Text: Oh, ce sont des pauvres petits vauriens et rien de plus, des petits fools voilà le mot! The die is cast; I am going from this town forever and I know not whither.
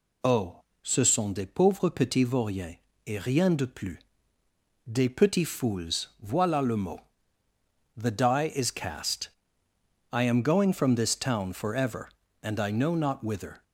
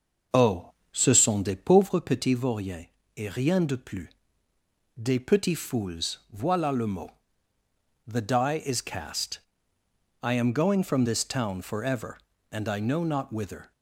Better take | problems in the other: first | starts louder than the rest; until 1.9 s; 6 dB // pauses between "vauriens" and "et"; slight; at 2.8 s; 0.32 s long; slight in the first

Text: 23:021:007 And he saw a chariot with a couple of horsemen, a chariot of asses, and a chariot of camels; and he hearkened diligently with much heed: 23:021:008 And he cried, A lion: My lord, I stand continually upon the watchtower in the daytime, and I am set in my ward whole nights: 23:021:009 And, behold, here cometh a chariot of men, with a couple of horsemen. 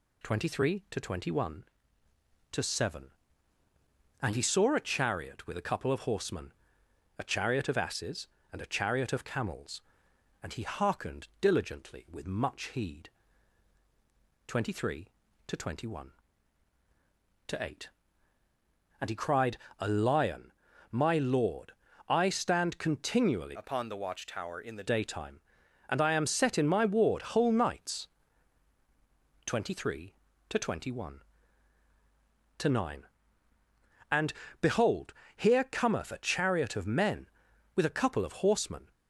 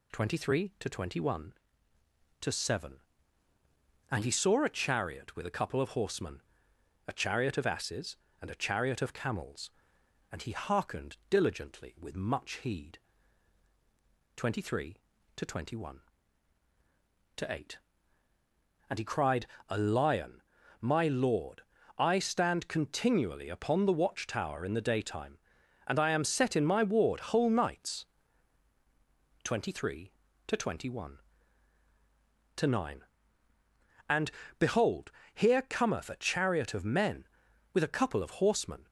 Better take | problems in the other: second | changes voice from "upon" to "the"; from 23.5 to 24.8 s; 1.3 s long

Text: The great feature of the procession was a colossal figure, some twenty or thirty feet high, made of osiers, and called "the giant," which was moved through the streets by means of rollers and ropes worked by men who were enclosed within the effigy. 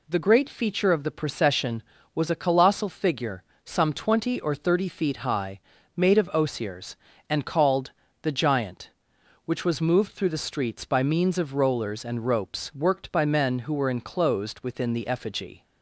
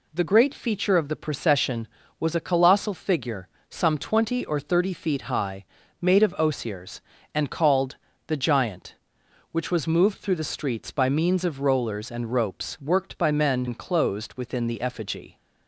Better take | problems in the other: first | pauses between "called" and "the"; slight; at 7.9 s; 0.28 s long; slight in the first // skips "who were"; at 13.6 s

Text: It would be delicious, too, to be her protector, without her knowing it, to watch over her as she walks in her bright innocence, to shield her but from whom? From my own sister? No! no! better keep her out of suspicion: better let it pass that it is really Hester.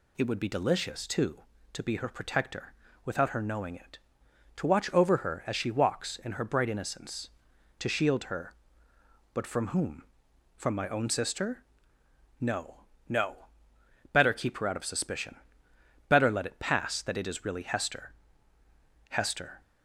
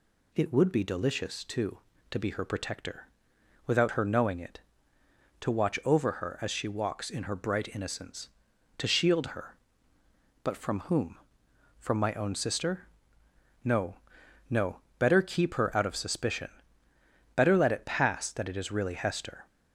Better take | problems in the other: second | goes on to say "Hester"; from 19.1 s on; 0.50 s long

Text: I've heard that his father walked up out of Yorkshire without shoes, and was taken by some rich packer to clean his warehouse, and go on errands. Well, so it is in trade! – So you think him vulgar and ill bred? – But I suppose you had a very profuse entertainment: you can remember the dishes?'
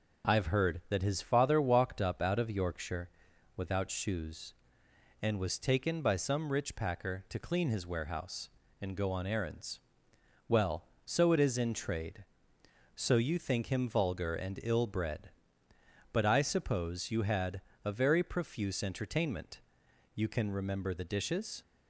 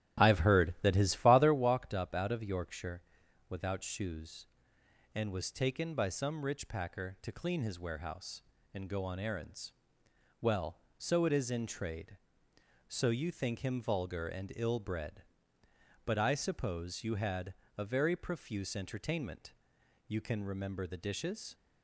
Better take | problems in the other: first | starts louder than the rest; strong; until 1.6 s; 12 dB // pauses between "Yorkshire" and "without"; noticeable; at 3.0 s; 0.48 s long; noticeable in the first // pauses between "had" and "a"; slight; at 17.5 s; 0.24 s long; slight in the first

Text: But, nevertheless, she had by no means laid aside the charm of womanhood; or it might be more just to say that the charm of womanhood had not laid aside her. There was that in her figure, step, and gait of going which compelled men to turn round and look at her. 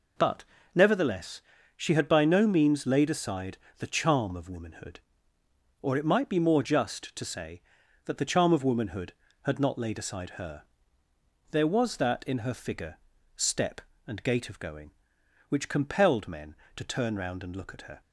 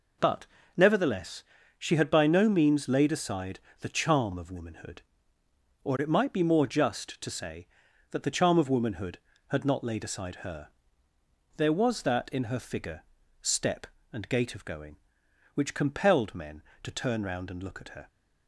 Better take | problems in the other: neither | pauses between "aside" and "the"; slight; the same in both

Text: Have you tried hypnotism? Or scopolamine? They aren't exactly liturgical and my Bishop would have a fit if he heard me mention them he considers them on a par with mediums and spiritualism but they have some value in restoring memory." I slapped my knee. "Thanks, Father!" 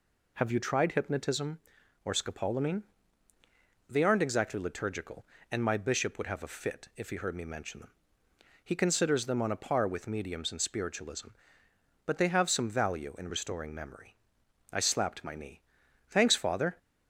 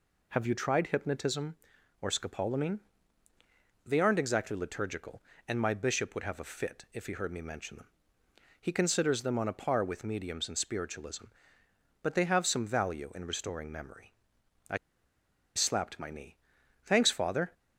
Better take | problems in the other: first | pauses between "them" and "he"; noticeable; at 7.8 s; 0.76 s long; noticeable in the first // pauses between "I" and "slapped"; noticeable; at 14.7 s; 0.79 s long

